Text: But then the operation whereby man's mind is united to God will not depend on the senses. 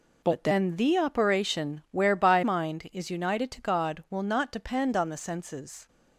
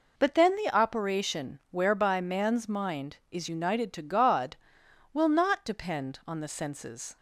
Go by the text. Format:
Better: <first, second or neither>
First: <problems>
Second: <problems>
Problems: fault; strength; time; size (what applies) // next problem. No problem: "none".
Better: second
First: skips "man's"; at 2.4 s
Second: none